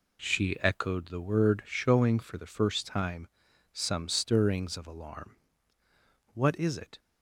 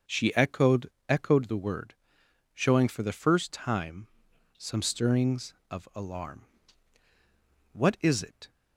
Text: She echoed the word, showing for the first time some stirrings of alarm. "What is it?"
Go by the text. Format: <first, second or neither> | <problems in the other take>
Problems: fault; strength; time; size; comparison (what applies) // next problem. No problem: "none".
first | says "echoed" twice; at 1.0 s // pauses between "time" and "some"; noticeable; at 4.0 s; 0.50 s long; also in the first